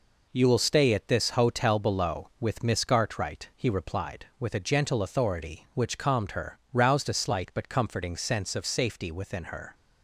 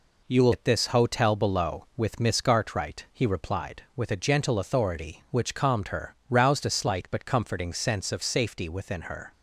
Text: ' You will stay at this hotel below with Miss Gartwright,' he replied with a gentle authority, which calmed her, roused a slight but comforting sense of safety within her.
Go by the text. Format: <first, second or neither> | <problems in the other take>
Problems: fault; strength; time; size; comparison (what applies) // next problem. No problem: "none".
first | skips "stay"; at 0.5 s